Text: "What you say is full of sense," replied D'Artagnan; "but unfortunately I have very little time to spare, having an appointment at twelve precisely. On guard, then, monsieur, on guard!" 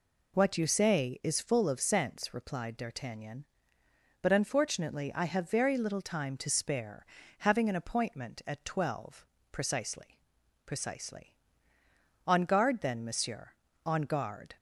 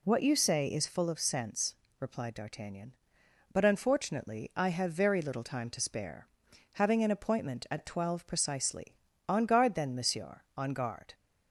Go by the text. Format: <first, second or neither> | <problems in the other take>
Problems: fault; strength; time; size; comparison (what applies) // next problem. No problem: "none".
second | pauses between "twelve" and "precisely"; slight; at 9.2 s; 0.28 s long // says "precisely" twice; at 10.6 s